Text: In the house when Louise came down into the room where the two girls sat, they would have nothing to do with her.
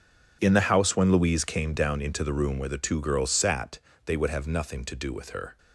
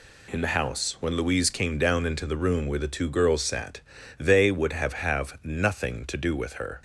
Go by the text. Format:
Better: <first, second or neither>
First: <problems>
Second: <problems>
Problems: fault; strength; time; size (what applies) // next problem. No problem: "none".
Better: first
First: none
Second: says "have" twice; at 4.9 s